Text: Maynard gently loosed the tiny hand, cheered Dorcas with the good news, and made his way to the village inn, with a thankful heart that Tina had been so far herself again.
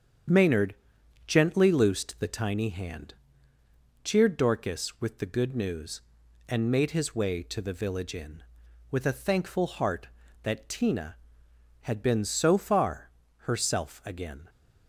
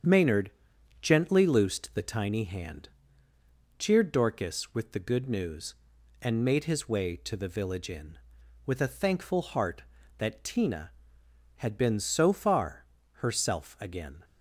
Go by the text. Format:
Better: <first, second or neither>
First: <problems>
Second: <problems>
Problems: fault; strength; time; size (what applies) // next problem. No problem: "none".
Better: neither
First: starts louder than the rest; strong; until 1.8 s; 7.5 dB // pauses between "Maynard" and "gently"; noticeable; at 0.7 s; 0.50 s long // pauses between "far" and "herself"; slight; at 13.0 s; 0.34 s long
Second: starts louder than the rest; strong; until 1.5 s; 7.5 dB // pauses between "Maynard" and "gently"; noticeable; at 0.5 s; 0.48 s long // pauses between "far" and "herself"; slight; at 12.8 s; 0.34 s long